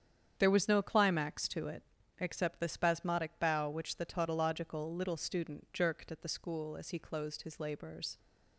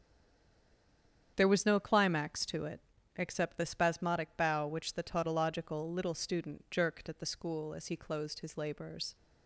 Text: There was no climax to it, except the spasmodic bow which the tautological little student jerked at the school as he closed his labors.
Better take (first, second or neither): first